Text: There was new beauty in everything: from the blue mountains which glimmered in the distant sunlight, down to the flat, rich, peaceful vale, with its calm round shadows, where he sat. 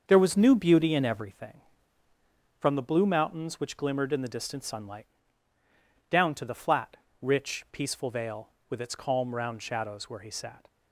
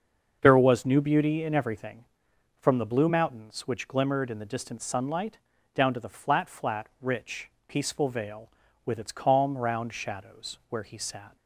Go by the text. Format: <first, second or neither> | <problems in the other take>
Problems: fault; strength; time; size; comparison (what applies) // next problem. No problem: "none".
first | starts louder than the rest; until 1.4 s; 6.5 dB; also in the first // says "flat" twice; at 6.4 s